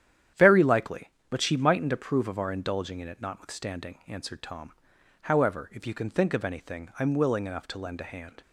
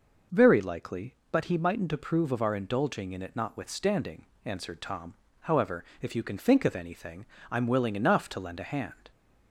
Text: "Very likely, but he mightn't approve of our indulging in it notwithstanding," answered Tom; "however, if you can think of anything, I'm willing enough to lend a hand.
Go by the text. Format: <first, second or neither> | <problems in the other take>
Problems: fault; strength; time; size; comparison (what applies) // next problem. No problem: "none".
second | starts louder than the rest; strong; until 1.5 s; 10 dB // says "she" for "he"; at 1.4 s